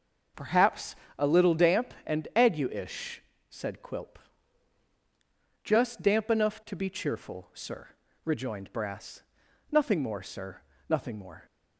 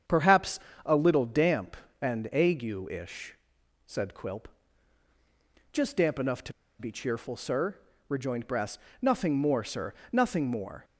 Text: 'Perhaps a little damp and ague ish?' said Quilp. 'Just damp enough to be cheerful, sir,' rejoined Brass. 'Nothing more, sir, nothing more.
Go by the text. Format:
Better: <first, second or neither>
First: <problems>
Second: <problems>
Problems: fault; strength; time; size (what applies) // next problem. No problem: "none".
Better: first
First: pauses between "Perhaps" and "a"; slight; at 0.9 s; 0.24 s long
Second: starts louder than the rest; strong; until 1.3 s; 8 dB // pauses between "Perhaps" and "a"; slight; at 0.5 s; 0.24 s long // pauses between "to" and "be"; slight; at 6.5 s; 0.27 s long